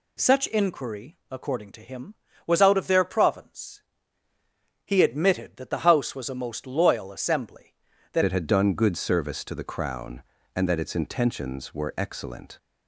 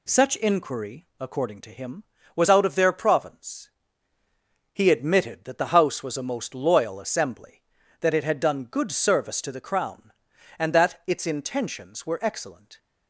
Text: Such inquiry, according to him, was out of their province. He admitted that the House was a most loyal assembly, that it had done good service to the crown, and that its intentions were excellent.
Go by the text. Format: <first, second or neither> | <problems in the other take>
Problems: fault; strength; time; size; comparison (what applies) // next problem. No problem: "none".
second | changes voice at "it"; from 8.2 s on; 4.3 s long